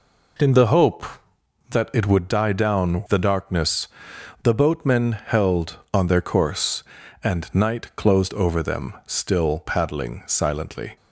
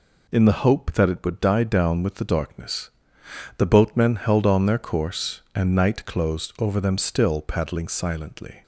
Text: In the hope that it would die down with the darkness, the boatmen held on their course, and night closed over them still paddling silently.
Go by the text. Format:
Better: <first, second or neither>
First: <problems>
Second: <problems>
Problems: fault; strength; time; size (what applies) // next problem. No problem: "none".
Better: second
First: skips "with"; at 3.0 s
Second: none